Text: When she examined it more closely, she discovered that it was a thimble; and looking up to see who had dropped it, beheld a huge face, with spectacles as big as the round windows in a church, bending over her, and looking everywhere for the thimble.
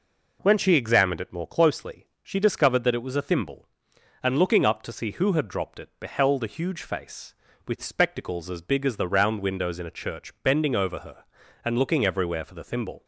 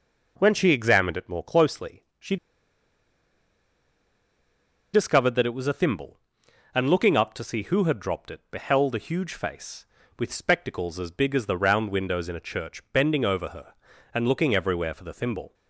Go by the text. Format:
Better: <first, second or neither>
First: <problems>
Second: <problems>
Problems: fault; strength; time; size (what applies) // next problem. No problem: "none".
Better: first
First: none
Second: pauses between "she" and "discovered"; strong; at 2.3 s; 2.5 s long